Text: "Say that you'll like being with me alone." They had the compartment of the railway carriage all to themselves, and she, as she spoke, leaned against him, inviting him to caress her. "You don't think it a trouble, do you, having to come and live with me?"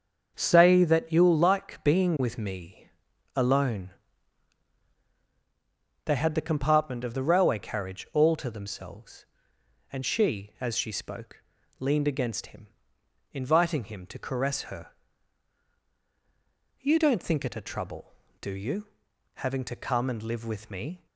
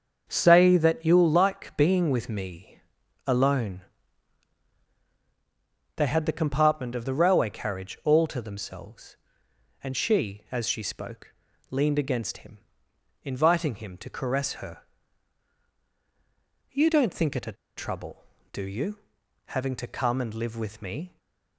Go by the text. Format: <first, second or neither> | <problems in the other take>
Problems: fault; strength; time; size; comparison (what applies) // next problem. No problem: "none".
first | starts louder than the rest; until 1.2 s; 6.5 dB; also in the first // pauses between "me" and "alone"; at 2.8 s; 0.44 s long; also in the first // pauses between "a" and "trouble"; slight; at 17.5 s; 0.23 s long // stays silent after the last word; slight; from 21.0 s on; 0.5 s long